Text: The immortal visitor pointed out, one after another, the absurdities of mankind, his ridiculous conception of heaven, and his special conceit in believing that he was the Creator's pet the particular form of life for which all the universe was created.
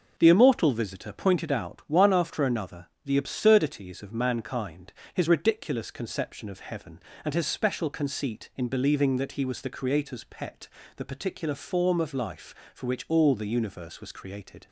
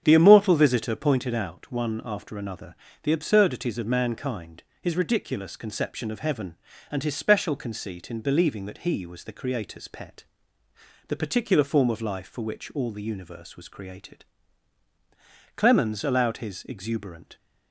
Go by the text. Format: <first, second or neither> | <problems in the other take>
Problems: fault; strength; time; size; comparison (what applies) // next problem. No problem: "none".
first | starts louder than the rest; strong; until 1.0 s; 8 dB // pauses between "pet" and "the"; noticeable; at 10.2 s; 0.84 s long; slight in the first // goes on to say "Clemens allowed his exuberant"; strong; from 15.5 s on; 1.7 s long